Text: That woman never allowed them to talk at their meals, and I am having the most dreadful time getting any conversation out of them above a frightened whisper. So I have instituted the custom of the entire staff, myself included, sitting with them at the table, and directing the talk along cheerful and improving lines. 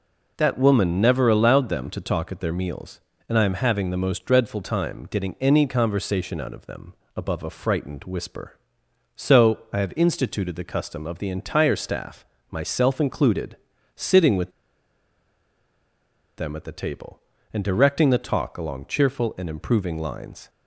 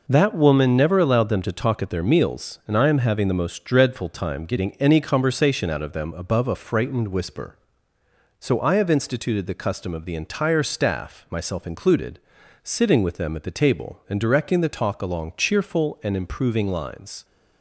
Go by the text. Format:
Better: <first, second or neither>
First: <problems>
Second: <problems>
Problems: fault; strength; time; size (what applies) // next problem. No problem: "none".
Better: second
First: pauses between "them" and "above"; slight; at 6.9 s; 0.20 s long // pauses between "with" and "them"; strong; at 14.4 s; 1.8 s long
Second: none